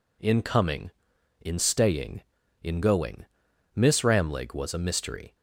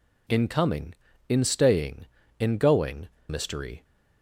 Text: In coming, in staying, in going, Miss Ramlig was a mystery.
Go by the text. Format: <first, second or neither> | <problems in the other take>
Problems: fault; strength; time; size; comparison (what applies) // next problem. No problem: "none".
first | skips "Miss Ramlig was a"; at 3.1 s